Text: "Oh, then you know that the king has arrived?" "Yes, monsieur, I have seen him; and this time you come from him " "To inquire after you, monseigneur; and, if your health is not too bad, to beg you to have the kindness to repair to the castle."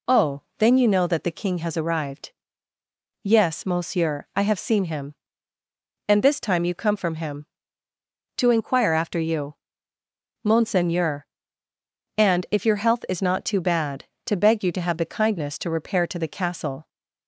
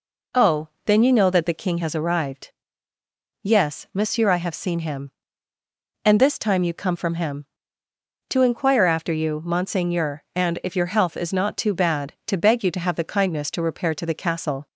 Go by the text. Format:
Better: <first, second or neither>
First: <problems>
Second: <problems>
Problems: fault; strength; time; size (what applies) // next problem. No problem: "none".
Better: neither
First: none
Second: none